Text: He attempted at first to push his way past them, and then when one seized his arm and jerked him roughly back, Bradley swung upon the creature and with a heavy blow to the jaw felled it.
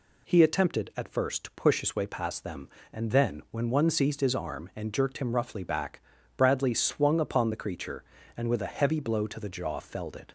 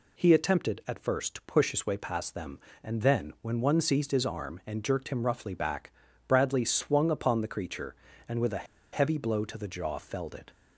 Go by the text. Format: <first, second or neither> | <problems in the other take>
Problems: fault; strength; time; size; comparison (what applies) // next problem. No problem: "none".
first | pauses between "a" and "heavy"; slight; at 8.6 s; 0.27 s long